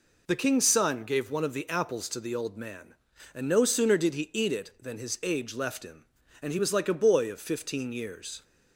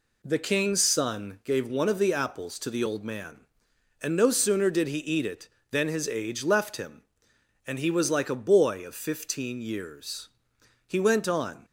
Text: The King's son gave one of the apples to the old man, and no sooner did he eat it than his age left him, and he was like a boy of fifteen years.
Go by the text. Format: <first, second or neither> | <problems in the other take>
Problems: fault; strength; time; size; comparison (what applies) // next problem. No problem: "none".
first | goes on to say "He went on"; noticeable; from 10.8 s on; 0.78 s long